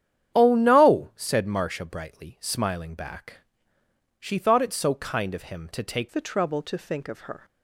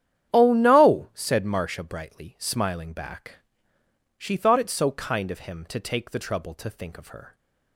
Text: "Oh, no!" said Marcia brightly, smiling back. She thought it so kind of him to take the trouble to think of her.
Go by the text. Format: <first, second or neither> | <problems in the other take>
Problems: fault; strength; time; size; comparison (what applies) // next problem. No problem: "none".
second | starts louder than the rest; strong; until 1.4 s; 9.5 dB; strong in the second // changes voice at "the"; from 6.0 s on; 1.4 s long